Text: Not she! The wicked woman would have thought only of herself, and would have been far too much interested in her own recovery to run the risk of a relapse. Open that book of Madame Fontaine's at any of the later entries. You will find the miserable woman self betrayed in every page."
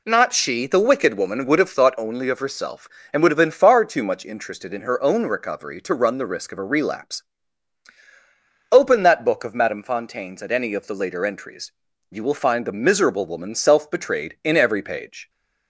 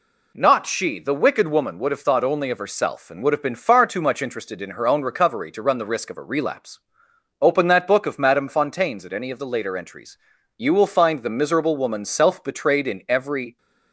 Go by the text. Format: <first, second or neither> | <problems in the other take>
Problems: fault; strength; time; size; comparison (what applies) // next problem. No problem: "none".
first | stops before "page"; at 13.5 s